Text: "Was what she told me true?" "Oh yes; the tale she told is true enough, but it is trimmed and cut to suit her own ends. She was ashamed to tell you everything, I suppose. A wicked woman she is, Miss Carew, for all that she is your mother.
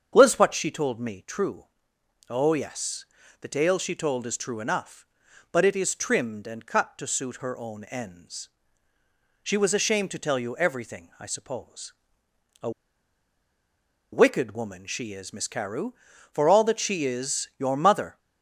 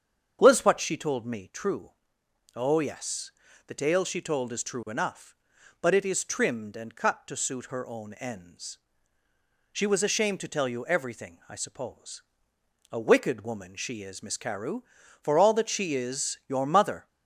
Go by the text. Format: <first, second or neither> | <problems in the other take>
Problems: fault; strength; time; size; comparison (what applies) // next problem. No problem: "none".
second | starts louder than the rest; strong; until 1.1 s; 7.5 dB; strong in the second // pauses between "A" and "wicked"; strong; at 12.6 s; 1.4 s long